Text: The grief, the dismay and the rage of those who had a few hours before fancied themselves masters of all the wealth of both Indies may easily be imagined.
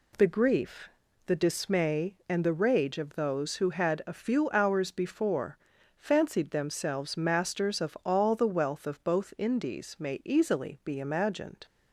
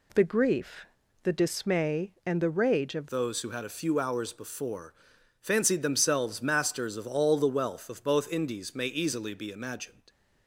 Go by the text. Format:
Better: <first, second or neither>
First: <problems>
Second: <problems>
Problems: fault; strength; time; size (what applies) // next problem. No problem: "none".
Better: first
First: pauses between "before" and "fancied"; at 5.5 s; 0.40 s long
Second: changes voice at "those"; from 3.1 s on; 6.9 s long // pauses between "before" and "fancied"; noticeable; at 4.9 s; 0.48 s long